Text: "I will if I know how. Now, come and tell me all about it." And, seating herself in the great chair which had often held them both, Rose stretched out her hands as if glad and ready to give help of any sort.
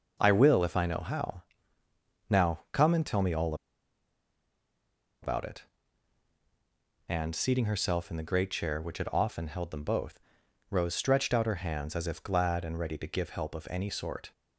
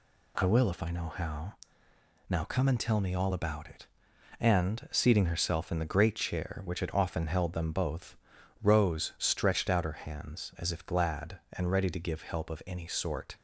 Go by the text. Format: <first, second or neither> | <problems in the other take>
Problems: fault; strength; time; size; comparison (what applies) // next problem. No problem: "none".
second | pauses between "all" and "about"; strong; at 3.5 s; 1.6 s long